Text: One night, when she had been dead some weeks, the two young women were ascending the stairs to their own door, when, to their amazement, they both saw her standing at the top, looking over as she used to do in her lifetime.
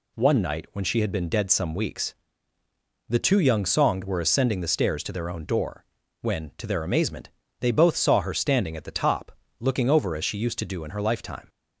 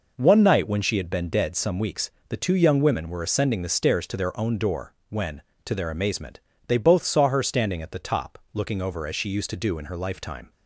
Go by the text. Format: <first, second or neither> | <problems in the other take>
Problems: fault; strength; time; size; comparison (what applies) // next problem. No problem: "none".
second | says "songed" for "women"; at 3.6 s